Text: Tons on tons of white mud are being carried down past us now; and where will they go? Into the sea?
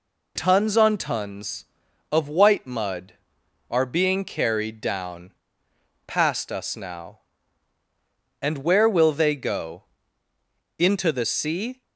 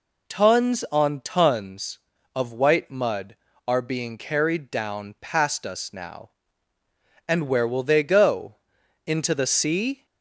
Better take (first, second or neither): second